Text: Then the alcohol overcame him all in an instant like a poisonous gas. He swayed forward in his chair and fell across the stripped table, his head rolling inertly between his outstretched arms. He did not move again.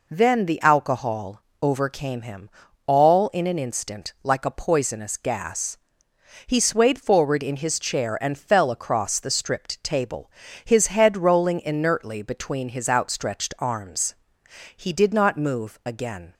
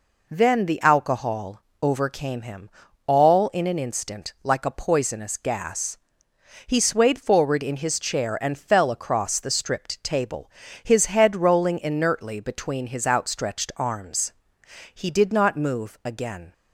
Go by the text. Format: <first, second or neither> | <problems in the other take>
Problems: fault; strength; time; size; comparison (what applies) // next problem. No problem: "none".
neither | pauses between "alcohol" and "overcame"; slight; the same in both // pauses between "him" and "all"; the same in both